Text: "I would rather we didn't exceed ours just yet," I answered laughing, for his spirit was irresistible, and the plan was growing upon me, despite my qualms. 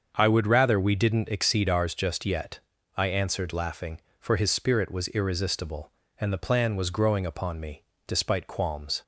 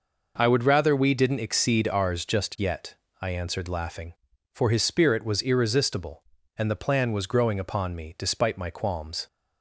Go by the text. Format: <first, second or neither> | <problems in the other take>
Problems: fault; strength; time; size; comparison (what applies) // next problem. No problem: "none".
second | starts louder than the rest; until 1.1 s; 6.5 dB // skips "my"; at 8.4 s